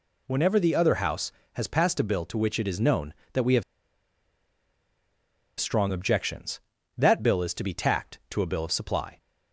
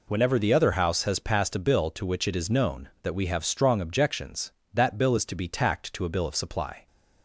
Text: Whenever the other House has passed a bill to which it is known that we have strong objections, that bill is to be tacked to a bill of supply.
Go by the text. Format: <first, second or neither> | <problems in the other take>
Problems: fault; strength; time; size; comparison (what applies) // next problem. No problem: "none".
second | pauses between "have" and "strong"; strong; at 3.6 s; 1.9 s long